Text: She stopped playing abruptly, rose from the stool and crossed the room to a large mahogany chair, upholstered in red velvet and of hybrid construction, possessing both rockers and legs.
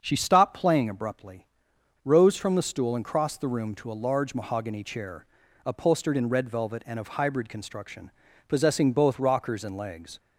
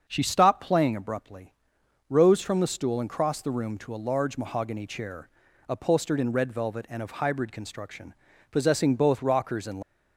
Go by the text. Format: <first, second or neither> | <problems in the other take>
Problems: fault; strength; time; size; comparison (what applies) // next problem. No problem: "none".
first | starts louder than the rest; until 1.0 s; 6.5 dB; also in the first // stops before "legs"; at 9.8 s